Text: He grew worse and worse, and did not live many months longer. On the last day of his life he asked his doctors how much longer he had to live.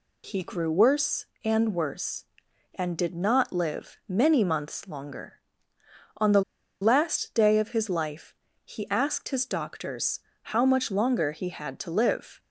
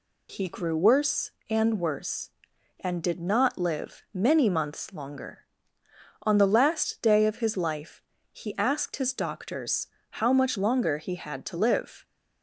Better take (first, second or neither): second